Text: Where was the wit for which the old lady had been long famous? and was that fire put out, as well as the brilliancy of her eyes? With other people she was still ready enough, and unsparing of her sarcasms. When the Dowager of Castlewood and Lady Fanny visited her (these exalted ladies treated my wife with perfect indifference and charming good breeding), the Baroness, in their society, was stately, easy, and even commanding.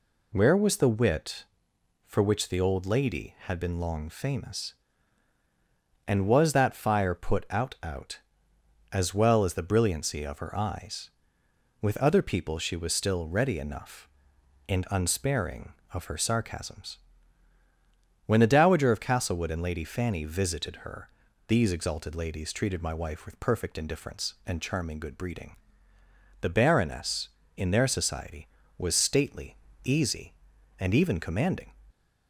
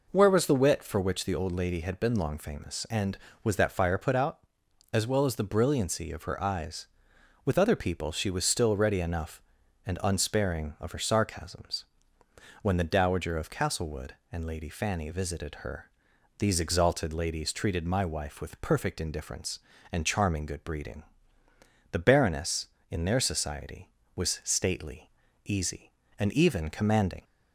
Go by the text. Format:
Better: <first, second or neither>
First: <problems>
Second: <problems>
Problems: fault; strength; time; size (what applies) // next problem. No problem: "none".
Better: second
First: says "out" twice; at 7.8 s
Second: none